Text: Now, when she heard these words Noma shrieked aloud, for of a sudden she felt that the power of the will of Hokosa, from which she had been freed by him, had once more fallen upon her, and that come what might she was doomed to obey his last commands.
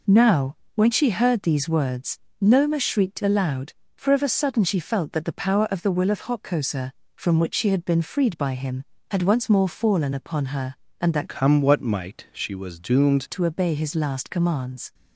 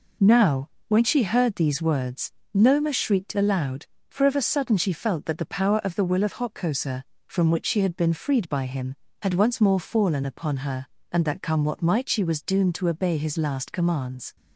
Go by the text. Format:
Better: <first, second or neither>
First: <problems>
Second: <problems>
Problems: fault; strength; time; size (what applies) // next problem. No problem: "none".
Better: second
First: pauses between "words" and "Noma"; slight; at 2.1 s; 0.20 s long // changes voice from "come" to "doomed"; from 11.2 to 13.2 s; 2.0 s long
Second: pauses between "words" and "Noma"; slight; at 2.3 s; 0.20 s long